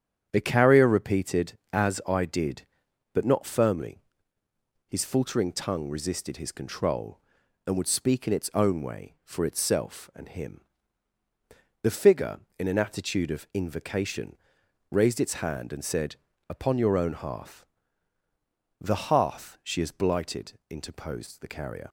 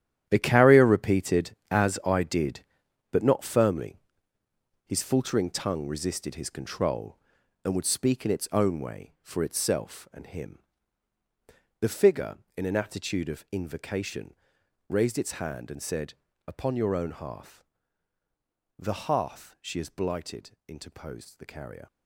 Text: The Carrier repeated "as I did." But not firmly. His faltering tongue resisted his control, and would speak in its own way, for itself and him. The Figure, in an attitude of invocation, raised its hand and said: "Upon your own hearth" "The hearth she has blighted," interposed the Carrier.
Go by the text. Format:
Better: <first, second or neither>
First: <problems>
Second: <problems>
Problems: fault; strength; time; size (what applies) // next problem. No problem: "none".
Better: first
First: starts louder than the rest; strong; until 1.3 s; 8.5 dB // pauses between "hearth" and "The"; at 17.6 s; 1.1 s long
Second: gets quieter; strong; throughout; 12.5 dB // starts louder than the rest; strong; until 1.2 s; 10.5 dB // pauses between "hearth" and "The"; at 17.6 s; 1.1 s long